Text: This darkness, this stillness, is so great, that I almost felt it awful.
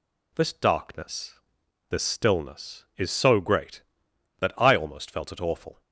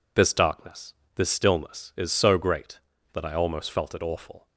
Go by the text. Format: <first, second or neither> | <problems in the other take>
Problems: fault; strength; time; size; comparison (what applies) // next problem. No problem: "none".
neither | none